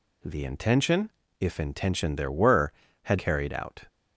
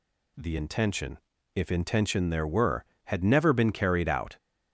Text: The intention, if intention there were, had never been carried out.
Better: second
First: skips "never been"; at 3.1 s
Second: none

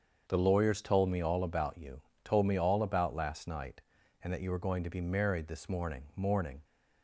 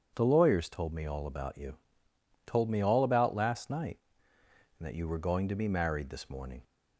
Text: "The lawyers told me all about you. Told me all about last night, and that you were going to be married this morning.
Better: second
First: starts louder than the rest; until 1.2 s; 7 dB // says "morning" twice; at 6.1 s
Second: none

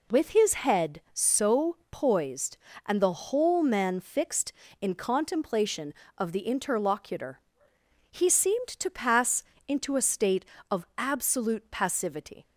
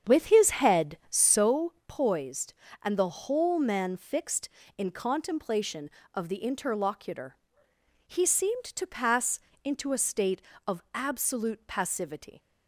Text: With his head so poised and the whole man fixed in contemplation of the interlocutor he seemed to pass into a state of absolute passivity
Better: first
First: pauses between "interlocutor" and "he"; noticeable; at 7.3 s; 0.72 s long // pauses between "pass" and "into"; slight; at 9.4 s; 0.24 s long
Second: starts louder than the rest; strong; until 1.5 s; 8 dB // pauses between "interlocutor" and "he"; noticeable; at 7.3 s; 0.72 s long // pauses between "pass" and "into"; slight; at 9.3 s; 0.24 s long

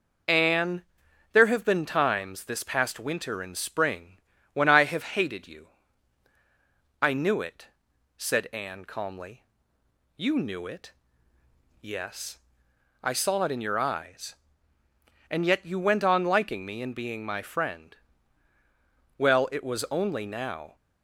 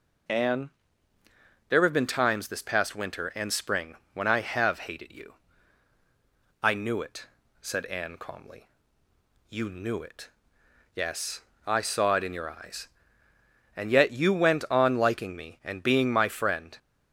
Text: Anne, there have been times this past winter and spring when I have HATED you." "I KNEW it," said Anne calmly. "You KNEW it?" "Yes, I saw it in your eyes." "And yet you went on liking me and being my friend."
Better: second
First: pauses between "spring" and "when"; slight; at 4.1 s; 0.34 s long // goes on to say "Well it was only now"; from 19.1 s on; 1.5 s long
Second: pauses between "spring" and "when"; slight; at 3.9 s; 0.20 s long

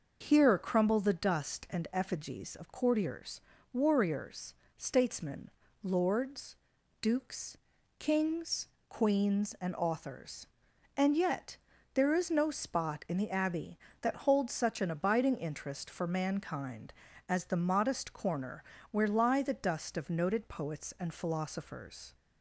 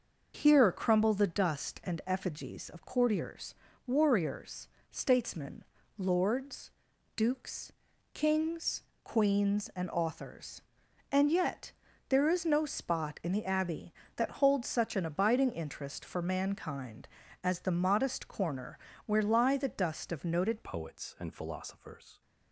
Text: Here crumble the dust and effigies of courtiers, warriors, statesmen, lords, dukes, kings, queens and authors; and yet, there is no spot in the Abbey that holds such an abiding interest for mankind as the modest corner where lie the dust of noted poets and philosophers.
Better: first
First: starts louder than the rest; until 1.3 s; 6 dB // pauses between "corner" and "where"; slight; at 18.6 s; 0.28 s long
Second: starts louder than the rest; until 1.4 s; 6 dB // pauses between "corner" and "where"; slight; at 18.7 s; 0.28 s long // changes voice at "poets"; from 20.6 s on; 1.6 s long

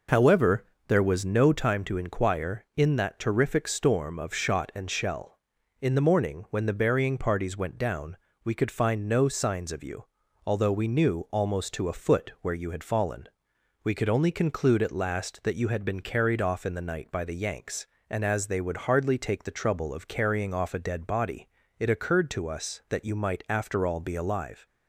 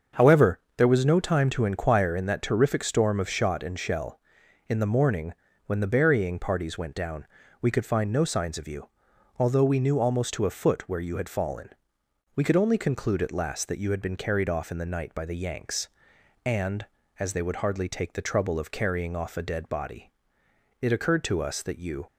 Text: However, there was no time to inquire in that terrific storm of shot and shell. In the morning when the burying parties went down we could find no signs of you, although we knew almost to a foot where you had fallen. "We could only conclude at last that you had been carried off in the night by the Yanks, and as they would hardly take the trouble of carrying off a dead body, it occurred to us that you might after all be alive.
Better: first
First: pauses between "down" and "we"; slight; at 8.1 s; 0.26 s long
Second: starts louder than the rest; until 1.3 s; 7 dB // pauses between "morning" and "when"; slight; at 5.3 s; 0.32 s long // pauses between "down" and "we"; slight; at 7.2 s; 0.34 s long // stops before "might after all be alive"; at 22.0 s

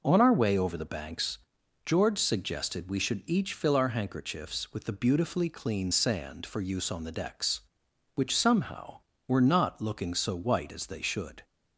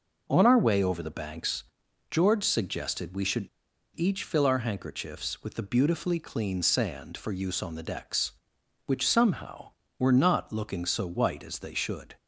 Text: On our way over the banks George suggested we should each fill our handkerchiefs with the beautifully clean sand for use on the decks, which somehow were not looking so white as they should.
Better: first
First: pauses between "banks" and "George"; noticeable; at 1.3 s; 0.48 s long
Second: pauses between "banks" and "George"; noticeable; at 1.6 s; 0.48 s long // pauses between "should" and "each"; noticeable; at 3.4 s; 0.48 s long

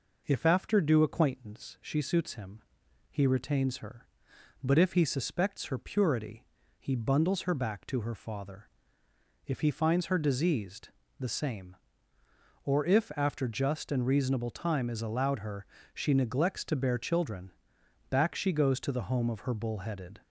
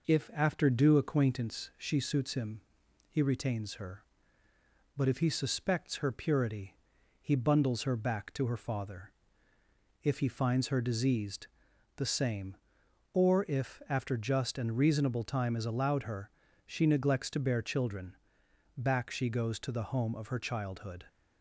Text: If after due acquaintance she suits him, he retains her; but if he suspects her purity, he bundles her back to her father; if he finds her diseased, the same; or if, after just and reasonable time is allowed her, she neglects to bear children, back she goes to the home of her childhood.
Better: second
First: says "bullheaded" for "childhood"; at 19.5 s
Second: none

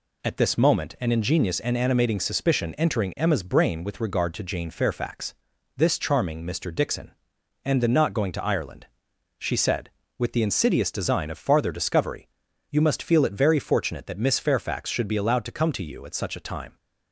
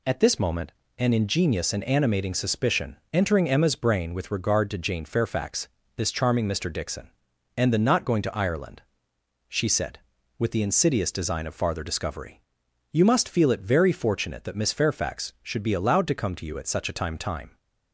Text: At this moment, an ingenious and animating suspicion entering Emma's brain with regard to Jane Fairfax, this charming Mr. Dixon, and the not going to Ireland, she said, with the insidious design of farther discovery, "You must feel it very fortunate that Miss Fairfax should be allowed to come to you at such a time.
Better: first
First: none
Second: pauses between "suspicion" and "entering"; slight; at 2.9 s; 0.16 s long // says "time" twice; at 17.1 s

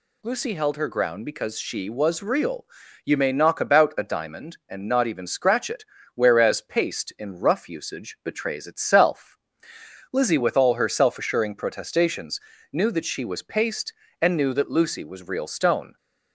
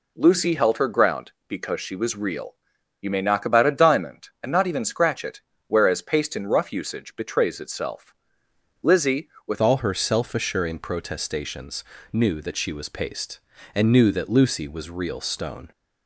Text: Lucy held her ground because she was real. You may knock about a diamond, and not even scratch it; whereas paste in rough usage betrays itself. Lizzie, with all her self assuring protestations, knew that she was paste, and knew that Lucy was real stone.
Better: first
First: none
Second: changes voice at "all"; from 9.6 s on; 6.1 s long

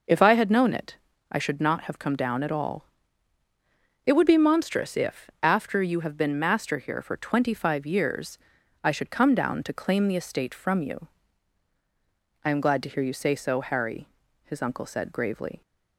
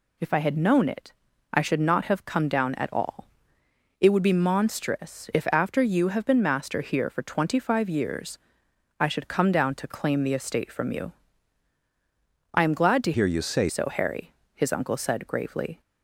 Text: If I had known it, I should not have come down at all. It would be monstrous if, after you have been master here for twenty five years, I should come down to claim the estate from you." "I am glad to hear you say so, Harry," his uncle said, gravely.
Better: first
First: none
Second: changes voice from "hear" to "say"; from 13.1 to 13.6 s; 0.5 s long

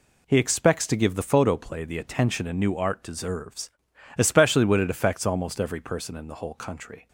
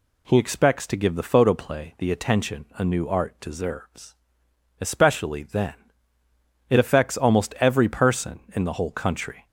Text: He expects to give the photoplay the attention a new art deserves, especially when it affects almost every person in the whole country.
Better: first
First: none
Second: says "then" for "when"; at 5.4 s

